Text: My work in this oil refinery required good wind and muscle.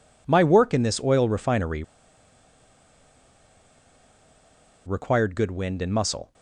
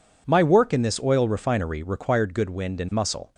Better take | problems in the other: second | pauses between "refinery" and "required"; strong; at 1.8 s; 3.0 s long

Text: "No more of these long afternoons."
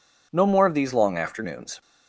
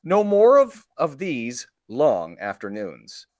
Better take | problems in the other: first | says "of" twice; at 0.9 s // pauses between "these" and "long"; slight; at 1.6 s; 0.20 s long

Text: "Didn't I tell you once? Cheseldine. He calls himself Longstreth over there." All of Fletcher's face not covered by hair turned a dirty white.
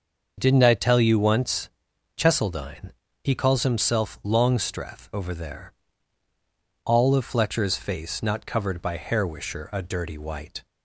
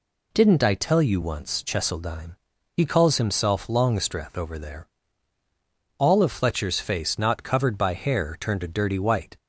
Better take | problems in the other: second | starts louder than the rest; until 1.3 s; 6.5 dB // says "wisher" for "turned"; at 9.2 s

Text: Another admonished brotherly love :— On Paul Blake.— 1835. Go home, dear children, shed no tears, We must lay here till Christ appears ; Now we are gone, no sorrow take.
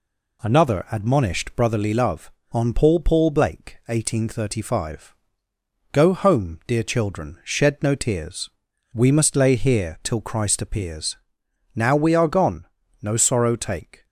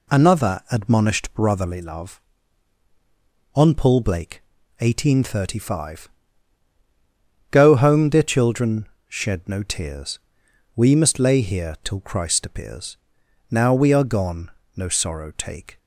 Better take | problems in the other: second | says "Paul" twice; at 2.9 s

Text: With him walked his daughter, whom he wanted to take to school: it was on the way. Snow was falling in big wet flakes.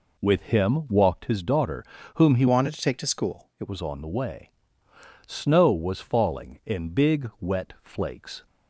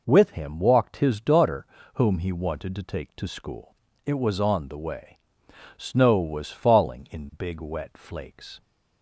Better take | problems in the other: second | changes voice from "wanted" to "it"; from 2.4 to 3.6 s; 1.2 s long

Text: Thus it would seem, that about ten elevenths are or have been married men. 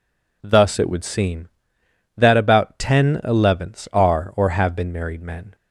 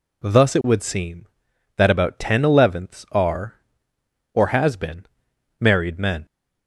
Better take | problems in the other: first | says "has" for "have"; at 4.4 s // pauses between "been" and "married"; noticeable; at 5.0 s; 0.54 s long

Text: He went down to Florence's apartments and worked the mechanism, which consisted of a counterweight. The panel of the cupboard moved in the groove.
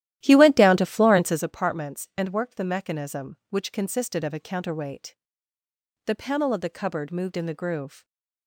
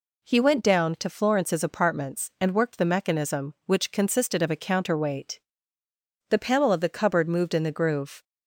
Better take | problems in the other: second | starts louder than the rest; strong; until 1.5 s; 13.5 dB

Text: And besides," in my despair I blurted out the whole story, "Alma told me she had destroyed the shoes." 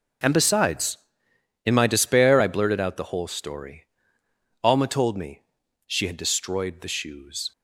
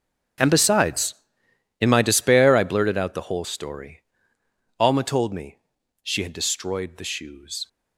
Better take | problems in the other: first | gets quieter; strong; throughout; 16.5 dB // pauses between "me" and "she"; noticeable; at 5.5 s; 0.46 s long; noticeable in the first

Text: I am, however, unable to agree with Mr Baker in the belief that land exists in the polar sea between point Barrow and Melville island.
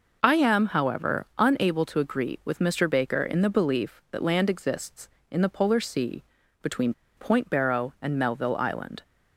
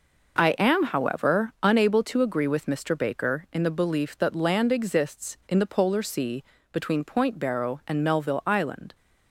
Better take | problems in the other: second | pauses between "sea" and "between"; slight; at 6.2 s; 0.36 s long; slight in the second // pauses between "between" and "point"; slight; at 6.9 s; 0.24 s long

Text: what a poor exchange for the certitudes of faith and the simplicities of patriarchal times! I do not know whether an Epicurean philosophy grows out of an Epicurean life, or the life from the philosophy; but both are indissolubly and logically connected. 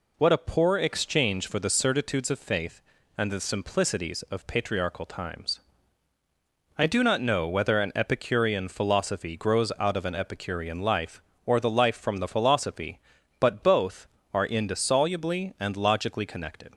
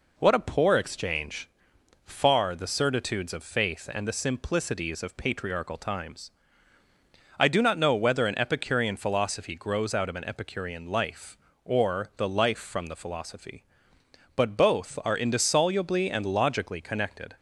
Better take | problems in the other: first | says "far" for "for"; at 2.0 s

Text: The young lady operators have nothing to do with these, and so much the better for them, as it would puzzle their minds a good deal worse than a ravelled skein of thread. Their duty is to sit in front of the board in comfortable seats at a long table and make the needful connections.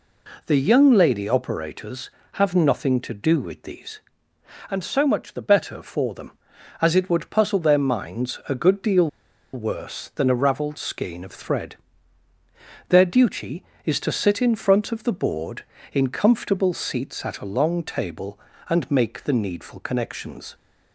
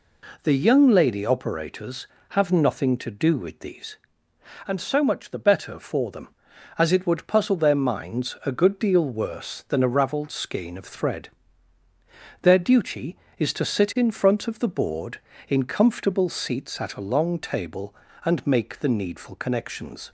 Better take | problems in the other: second | pauses between "deal" and "worse"; noticeable; at 9.0 s; 0.46 s long

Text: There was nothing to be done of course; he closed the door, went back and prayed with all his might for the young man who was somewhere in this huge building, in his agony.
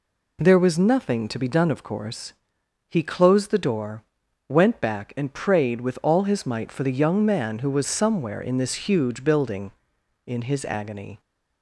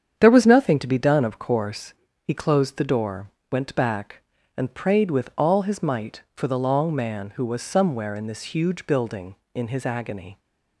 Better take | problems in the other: first | starts louder than the rest; strong; until 1.1 s; 8 dB // says "long" for "young"; at 6.5 s

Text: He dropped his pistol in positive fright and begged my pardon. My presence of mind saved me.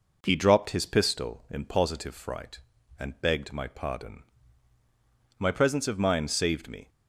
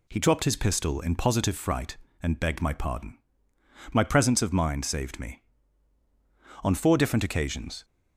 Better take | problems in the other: first | goes on to say "On four different occasions"; noticeable; from 6.6 s on; 1.2 s long

